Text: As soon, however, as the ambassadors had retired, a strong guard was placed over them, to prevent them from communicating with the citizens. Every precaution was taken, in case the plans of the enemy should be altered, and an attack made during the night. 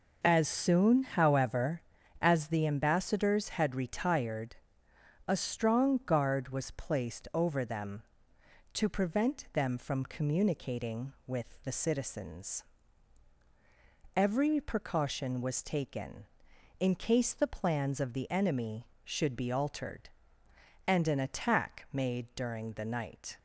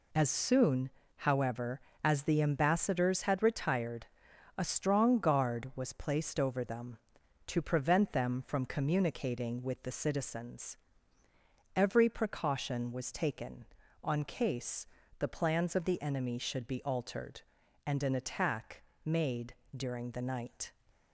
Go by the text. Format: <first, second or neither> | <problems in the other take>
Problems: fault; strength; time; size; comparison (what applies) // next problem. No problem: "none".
first | says "on" for "in"; at 14.0 s // pauses between "case" and "the"; slight; at 14.8 s; 0.32 s long // pauses between "attack" and "made"; slight; at 18.8 s; 0.22 s long // pauses between "made" and "during"; slight; at 19.5 s; 0.22 s long